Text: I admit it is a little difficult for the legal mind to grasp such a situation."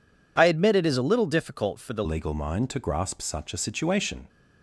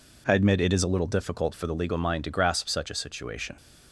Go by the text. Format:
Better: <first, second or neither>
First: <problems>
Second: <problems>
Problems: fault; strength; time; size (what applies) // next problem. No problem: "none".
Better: second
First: changes voice at "legal"; from 2.0 s on; 2.2 s long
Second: none